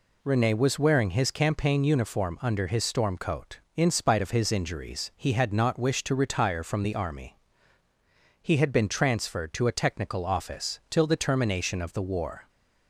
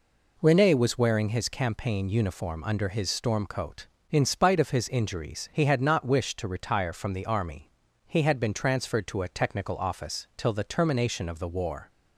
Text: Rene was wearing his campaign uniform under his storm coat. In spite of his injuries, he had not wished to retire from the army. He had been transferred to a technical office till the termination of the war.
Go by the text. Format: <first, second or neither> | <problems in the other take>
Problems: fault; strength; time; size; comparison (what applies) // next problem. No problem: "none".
neither | none